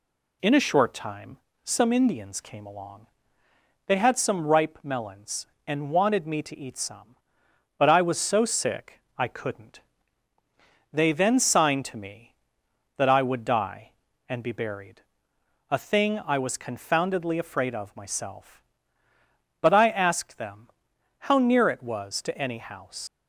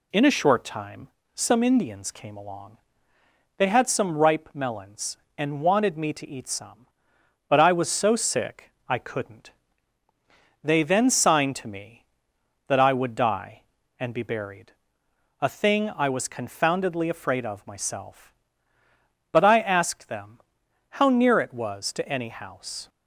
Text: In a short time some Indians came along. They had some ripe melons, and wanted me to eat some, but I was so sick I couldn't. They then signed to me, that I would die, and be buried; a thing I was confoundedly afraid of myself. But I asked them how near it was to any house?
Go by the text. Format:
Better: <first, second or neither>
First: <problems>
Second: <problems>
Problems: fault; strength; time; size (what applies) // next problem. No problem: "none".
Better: second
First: pauses between "time" and "some"; slight; at 1.3 s; 0.26 s long // pauses between "sick" and "I"; slight; at 8.9 s; 0.18 s long // pauses between "them" and "how"; noticeable; at 20.6 s; 0.58 s long // leaves "house" unfinished; at 23.0 s; 105 ms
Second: pauses between "time" and "some"; slight; at 1.0 s; 0.26 s long // pauses between "sick" and "I"; slight; at 8.7 s; 0.18 s long // pauses between "them" and "how"; noticeable; at 20.4 s; 0.58 s long